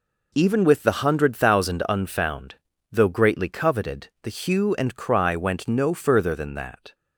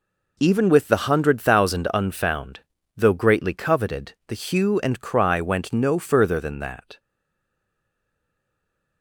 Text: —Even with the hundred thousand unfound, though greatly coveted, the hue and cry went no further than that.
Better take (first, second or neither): first